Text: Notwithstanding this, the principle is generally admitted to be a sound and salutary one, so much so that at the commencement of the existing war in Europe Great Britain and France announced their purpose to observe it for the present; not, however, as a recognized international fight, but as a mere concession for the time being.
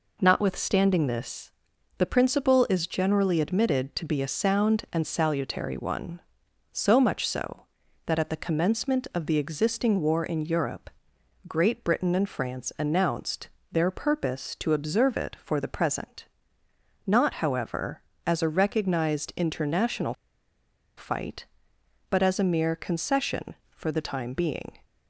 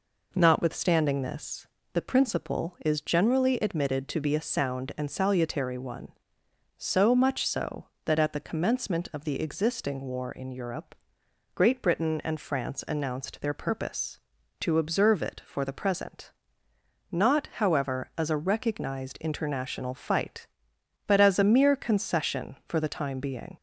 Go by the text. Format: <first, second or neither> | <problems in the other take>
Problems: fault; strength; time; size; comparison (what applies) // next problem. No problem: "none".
second | pauses between "Europe" and "Great"; noticeable; at 10.8 s; 0.58 s long; noticeable in the second // pauses between "announced" and "their"; slight; at 13.4 s; 0.24 s long // pauses between "international" and "fight"; noticeable; at 20.1 s; 0.84 s long